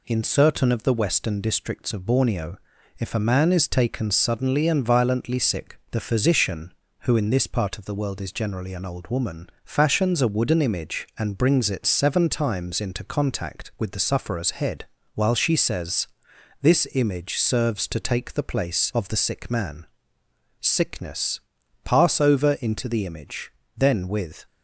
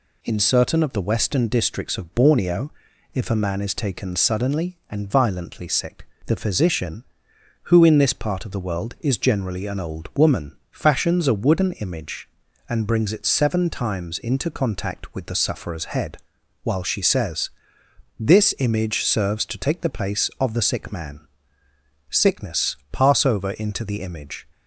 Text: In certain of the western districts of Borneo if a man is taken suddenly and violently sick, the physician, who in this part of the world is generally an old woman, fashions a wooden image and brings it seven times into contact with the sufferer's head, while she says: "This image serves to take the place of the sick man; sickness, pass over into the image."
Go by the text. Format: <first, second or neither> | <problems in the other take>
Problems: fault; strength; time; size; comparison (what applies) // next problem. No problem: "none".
second | pauses between "Borneo" and "if"; at 2.5 s; 0.40 s long; also in the second // goes on to say "Then with"; noticeable; from 23.7 s on; 0.68 s long